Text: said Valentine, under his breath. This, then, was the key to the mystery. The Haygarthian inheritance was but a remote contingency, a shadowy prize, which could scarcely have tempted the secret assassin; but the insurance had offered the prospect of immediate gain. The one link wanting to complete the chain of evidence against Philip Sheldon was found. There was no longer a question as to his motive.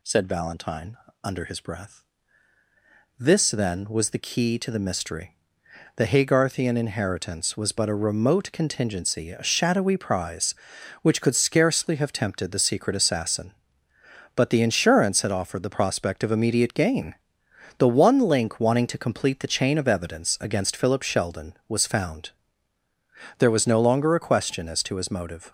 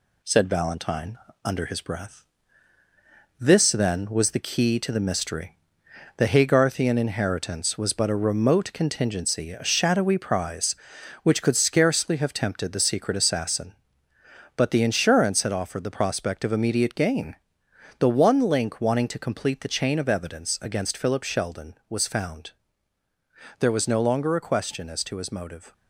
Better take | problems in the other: first | gets quieter; slight; throughout; 3 dB

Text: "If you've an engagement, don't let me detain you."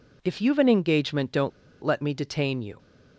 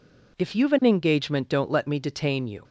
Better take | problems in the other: second | pauses between "don't" and "let"; slight; at 1.5 s; 0.34 s long

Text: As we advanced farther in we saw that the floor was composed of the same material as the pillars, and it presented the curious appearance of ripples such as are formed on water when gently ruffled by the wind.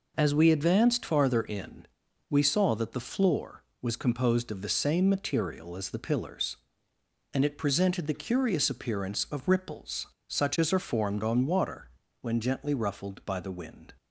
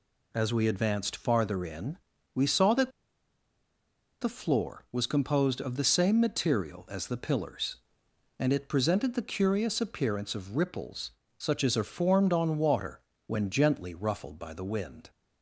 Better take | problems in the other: first | pauses between "in" and "we"; slight; at 1.9 s; 0.36 s long; also in the first // pauses between "that" and "the"; strong; at 2.8 s; 1.3 s long // pauses between "ripples" and "such"; slight; at 11.1 s; 0.26 s long; slight in the first // pauses between "water" and "when"; slight; at 12.9 s; 0.28 s long; slight in the first

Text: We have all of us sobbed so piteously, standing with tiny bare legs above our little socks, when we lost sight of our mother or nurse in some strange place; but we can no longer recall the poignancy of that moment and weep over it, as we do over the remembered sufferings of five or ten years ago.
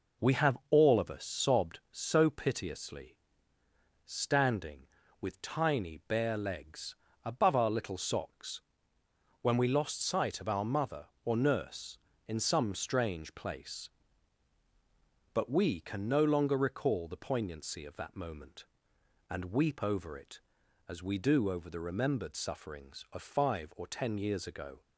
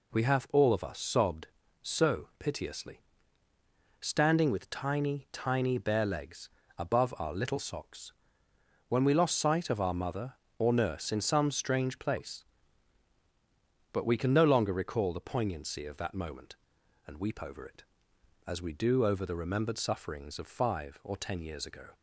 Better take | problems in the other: first | says "tiny" twice; at 5.3 s // pauses between "legs" and "above"; slight; at 6.4 s; 0.28 s long; slight in the first

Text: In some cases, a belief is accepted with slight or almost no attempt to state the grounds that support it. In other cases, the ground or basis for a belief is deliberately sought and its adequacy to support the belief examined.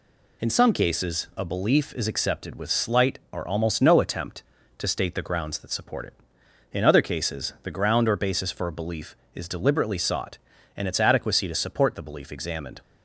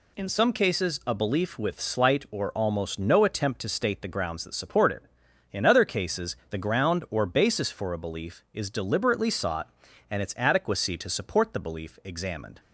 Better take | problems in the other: first | skips "is accepted"; at 1.5 s

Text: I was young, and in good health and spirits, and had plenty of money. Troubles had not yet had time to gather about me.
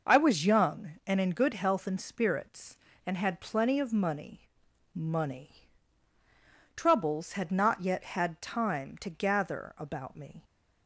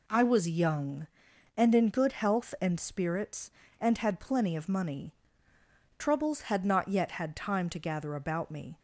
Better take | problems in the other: second | says "money" twice; at 4.9 s

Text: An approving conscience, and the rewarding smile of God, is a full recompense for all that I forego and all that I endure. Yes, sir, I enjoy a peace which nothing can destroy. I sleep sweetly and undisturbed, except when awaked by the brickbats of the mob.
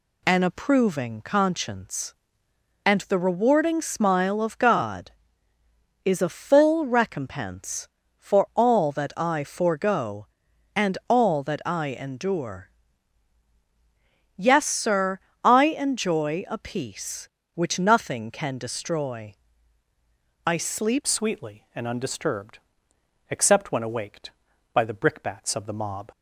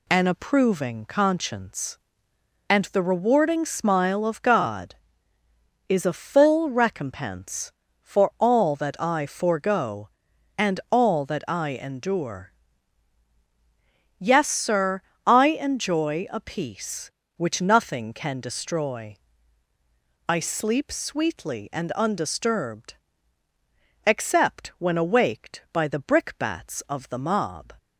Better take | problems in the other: second | changes voice at "sweetly"; from 21.0 s on; 5.1 s long

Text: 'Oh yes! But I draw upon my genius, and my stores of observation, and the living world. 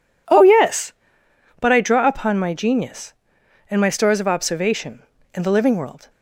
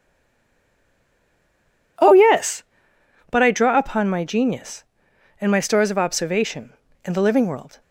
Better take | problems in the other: first | stays silent before the first word; noticeable; until 1.9 s; 1.9 s long

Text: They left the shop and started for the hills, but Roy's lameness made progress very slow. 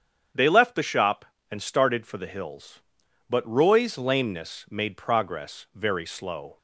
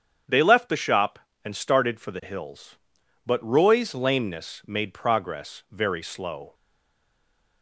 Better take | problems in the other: first | starts louder than the rest; strong; until 1.5 s; 8 dB; strong in the first // stays silent after the last word; from 6.5 s on; 1.1 s long

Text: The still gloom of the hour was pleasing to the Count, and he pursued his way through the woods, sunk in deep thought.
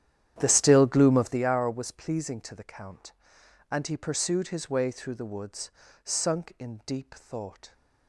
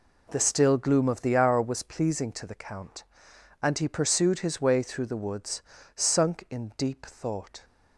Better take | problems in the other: second | starts louder than the rest; strong; until 1.4 s; 10.5 dB

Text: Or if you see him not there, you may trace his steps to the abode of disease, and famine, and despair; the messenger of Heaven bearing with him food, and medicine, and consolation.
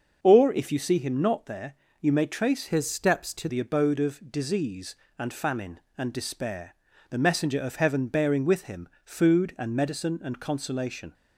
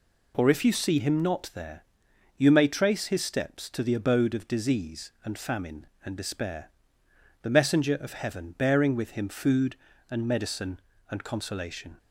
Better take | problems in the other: second | starts louder than the rest; until 1.2 s; 6 dB // changes voice from "his" to "to"; from 2.6 to 3.4 s; 0.8 s long // pauses between "him" and "food"; slight; at 8.8 s; 0.16 s long

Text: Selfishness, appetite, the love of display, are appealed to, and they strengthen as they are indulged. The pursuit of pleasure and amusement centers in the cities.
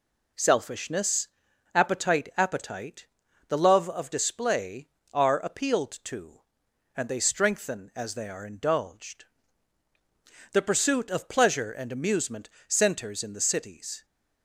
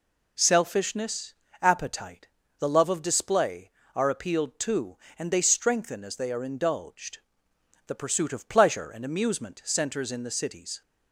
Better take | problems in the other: second | says "appetite" twice; at 2.3 s // pauses between "amusement" and "centers"; slight; at 12.4 s; 0.18 s long

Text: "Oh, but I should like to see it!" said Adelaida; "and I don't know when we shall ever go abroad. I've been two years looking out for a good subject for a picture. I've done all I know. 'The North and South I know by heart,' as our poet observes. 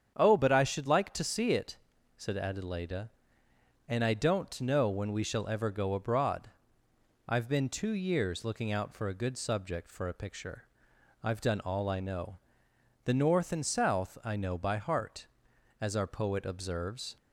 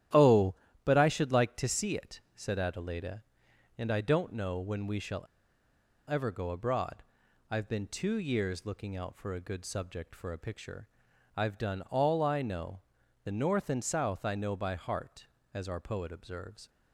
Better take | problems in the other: first | starts louder than the rest; strong; until 1.4 s; 12.5 dB; strong in the first // pauses between "shall" and "ever"; noticeable; at 5.2 s; 0.83 s long

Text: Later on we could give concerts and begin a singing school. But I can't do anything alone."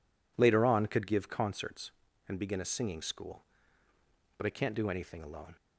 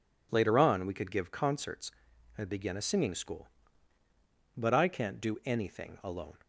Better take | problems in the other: second | skips "we"; at 0.8 s

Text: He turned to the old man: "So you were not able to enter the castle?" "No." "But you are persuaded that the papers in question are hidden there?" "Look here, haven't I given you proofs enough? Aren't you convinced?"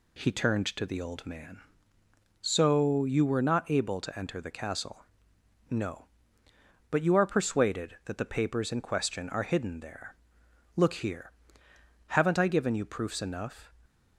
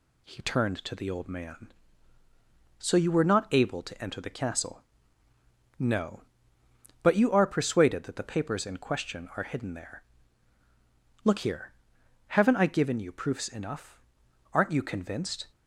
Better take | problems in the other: second | stops before "Aren't you convinced"; at 13.8 s

